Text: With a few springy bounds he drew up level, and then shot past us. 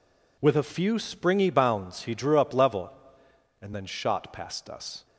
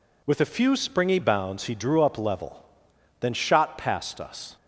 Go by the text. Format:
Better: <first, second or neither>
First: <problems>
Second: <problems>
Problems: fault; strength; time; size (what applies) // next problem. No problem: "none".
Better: first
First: none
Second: skips "and"; at 2.9 s